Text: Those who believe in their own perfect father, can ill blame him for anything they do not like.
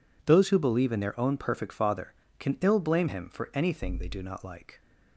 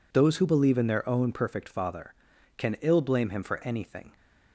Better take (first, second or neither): first